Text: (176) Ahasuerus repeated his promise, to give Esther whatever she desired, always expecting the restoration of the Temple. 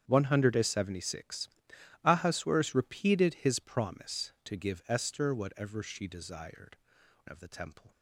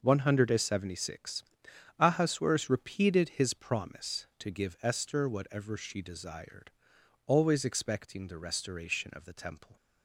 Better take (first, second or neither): second